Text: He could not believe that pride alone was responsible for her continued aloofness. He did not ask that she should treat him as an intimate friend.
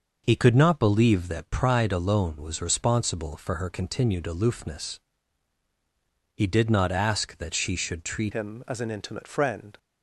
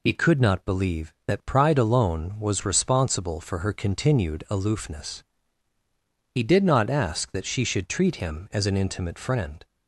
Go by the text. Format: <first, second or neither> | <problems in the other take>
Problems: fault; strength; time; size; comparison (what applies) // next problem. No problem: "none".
second | changes voice at "him"; from 8.3 s on; 1.4 s long